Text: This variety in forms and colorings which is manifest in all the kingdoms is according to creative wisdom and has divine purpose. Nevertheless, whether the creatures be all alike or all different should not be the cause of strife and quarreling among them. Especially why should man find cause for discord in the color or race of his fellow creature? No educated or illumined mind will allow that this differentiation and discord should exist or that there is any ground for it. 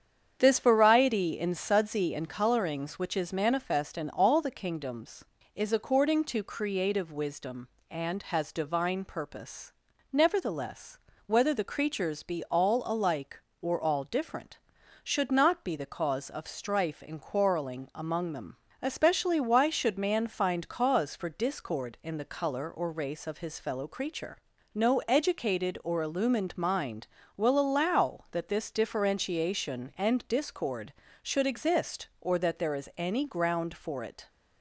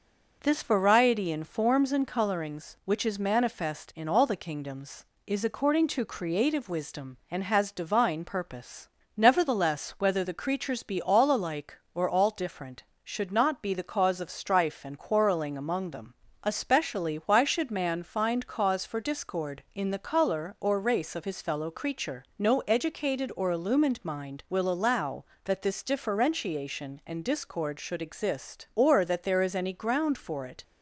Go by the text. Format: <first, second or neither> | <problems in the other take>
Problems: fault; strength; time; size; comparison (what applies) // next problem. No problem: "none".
second | starts louder than the rest; strong; until 1.4 s; 8 dB // says "sudsy" for "forms"; at 1.5 s